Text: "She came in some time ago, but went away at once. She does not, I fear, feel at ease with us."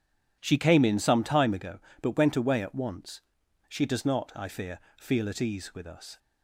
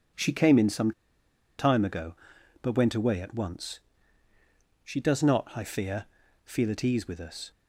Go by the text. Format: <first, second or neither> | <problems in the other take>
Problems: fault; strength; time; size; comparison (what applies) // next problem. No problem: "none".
first | pauses between "some" and "time"; noticeable; at 0.9 s; 0.67 s long